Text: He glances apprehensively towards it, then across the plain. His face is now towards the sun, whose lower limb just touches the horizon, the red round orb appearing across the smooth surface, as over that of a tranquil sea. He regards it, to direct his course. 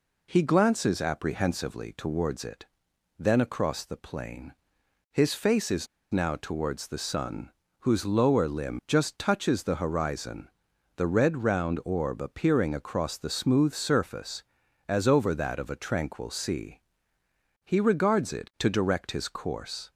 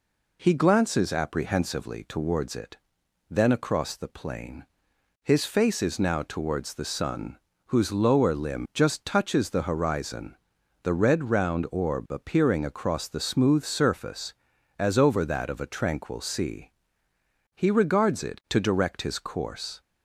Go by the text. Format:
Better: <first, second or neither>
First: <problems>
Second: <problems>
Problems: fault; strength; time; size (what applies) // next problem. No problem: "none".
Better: second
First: pauses between "is" and "now"; slight; at 5.8 s; 0.25 s long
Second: none